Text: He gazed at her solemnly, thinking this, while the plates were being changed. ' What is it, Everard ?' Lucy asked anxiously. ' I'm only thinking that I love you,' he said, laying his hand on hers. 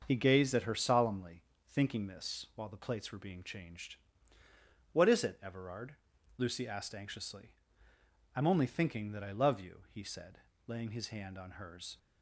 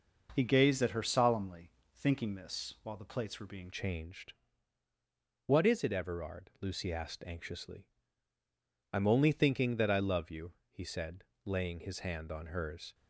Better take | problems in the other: first | starts louder than the rest; until 1.3 s; 6.5 dB; also in the first // changes voice at "changed"; from 3.7 s on; 9.2 s long

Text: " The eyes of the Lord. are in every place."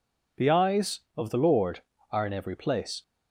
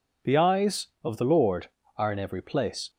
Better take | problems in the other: neither | none

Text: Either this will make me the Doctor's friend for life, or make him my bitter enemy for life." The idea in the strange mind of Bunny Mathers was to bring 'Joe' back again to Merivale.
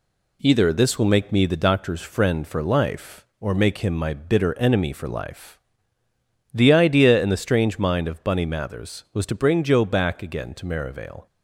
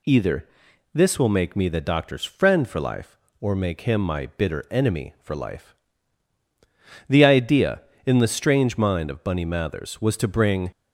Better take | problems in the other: first | pauses between "Either" and "this"; noticeable; at 0.4 s; 0.46 s long // stops before "Joe back again to Merivale"; at 10.7 s

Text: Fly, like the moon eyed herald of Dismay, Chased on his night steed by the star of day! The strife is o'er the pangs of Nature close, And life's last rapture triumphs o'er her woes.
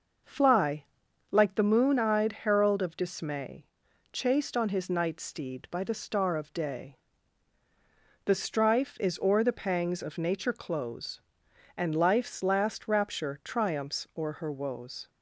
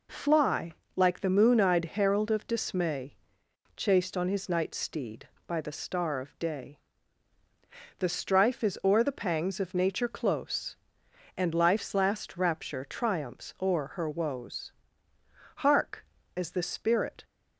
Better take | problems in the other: first | goes on to say "Hark as the spirit"; from 15.5 s on; 1.6 s long

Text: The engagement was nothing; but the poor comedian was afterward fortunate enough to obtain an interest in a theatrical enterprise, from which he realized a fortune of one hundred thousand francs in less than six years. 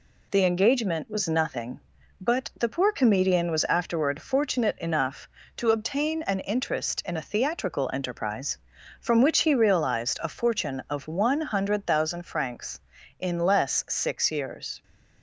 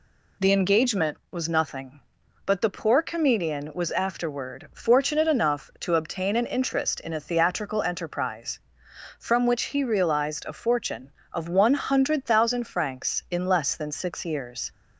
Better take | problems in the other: second | skips "than"; at 13.8 s

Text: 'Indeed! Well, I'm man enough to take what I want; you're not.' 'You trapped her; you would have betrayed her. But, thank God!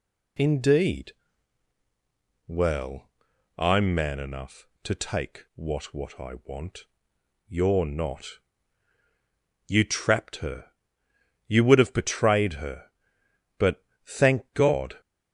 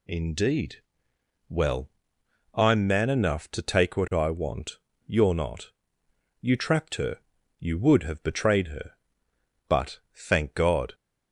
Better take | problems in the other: second | says "what" twice; at 5.9 s

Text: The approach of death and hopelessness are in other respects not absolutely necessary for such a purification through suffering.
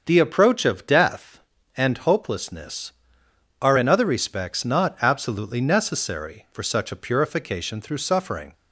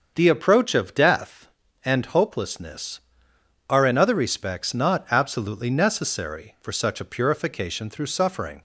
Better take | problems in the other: neither | starts louder than the rest; the same in both

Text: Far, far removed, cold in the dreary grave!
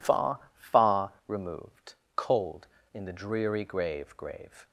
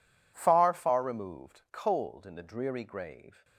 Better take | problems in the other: second | pauses between "far" and "removed"; slight; at 1.1 s; 0.16 s long // says "grave" twice; at 4.1 s

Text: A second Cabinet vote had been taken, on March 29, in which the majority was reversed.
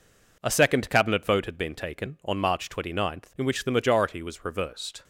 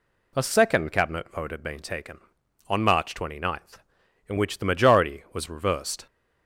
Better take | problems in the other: second | gets quieter; noticeable; throughout; 5 dB

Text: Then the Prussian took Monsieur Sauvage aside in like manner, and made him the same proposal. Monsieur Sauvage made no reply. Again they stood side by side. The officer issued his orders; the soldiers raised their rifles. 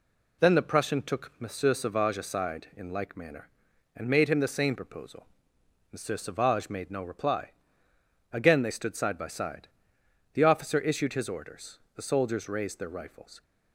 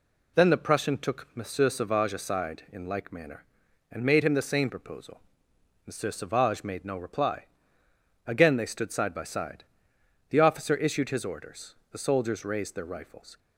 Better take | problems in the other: neither | none

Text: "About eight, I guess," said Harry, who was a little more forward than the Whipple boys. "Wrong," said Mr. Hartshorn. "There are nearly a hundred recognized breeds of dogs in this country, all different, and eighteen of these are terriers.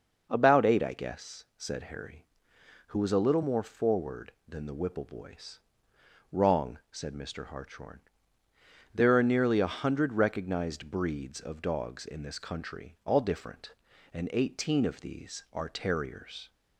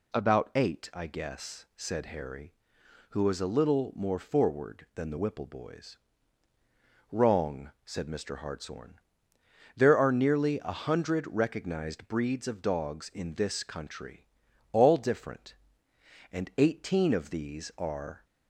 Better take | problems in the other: first | stops before "terriers"; at 18.2 s

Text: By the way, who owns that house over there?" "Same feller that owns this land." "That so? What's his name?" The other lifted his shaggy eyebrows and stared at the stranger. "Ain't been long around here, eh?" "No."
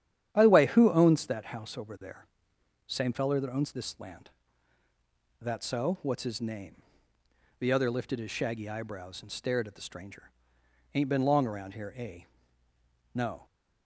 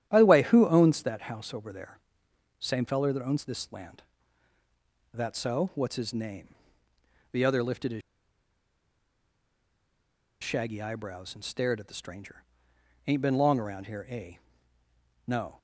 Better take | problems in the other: first | starts louder than the rest; strong; until 1.1 s; 10 dB; strong in the first // pauses between "his" and "shaggy"; strong; at 8.0 s; 2.4 s long

